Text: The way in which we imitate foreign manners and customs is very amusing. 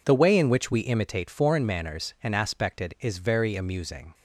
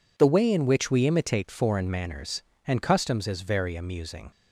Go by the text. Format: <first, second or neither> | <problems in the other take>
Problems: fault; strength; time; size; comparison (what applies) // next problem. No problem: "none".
second | says "aspected" for "customs"; at 2.3 s